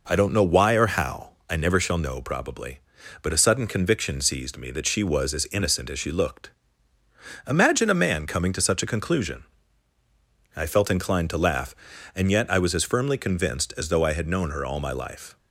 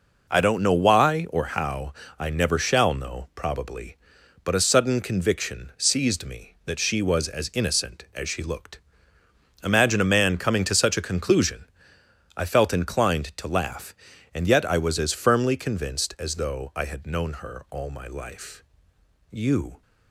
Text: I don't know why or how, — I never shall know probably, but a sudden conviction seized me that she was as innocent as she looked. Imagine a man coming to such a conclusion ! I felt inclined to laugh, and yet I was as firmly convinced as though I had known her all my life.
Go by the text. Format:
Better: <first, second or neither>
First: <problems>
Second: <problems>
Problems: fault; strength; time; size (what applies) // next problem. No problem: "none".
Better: first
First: none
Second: goes on to say "You"; from 19.3 s on; 0.50 s long